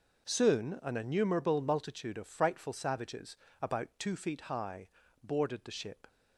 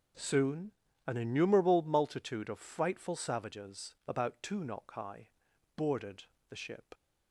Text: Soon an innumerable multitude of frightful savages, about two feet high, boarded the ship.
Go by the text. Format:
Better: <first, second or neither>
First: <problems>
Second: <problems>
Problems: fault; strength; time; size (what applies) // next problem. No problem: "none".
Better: first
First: none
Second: pauses between "Soon" and "an"; slight; at 0.7 s; 0.34 s long // says "knock" for "feet"; at 4.6 s // pauses between "boarded" and "the"; slight; at 6.2 s; 0.26 s long